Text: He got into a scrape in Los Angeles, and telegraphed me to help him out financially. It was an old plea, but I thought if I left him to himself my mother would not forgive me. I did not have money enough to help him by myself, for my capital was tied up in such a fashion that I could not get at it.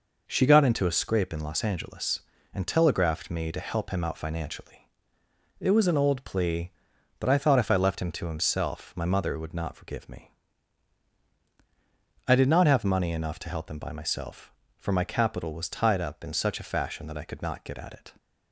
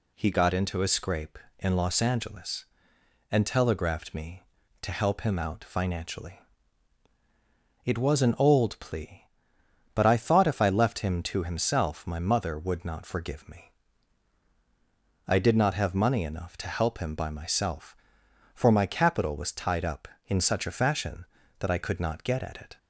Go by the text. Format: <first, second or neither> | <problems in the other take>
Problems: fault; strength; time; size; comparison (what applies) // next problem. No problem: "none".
second | says "She" for "He"; at 0.2 s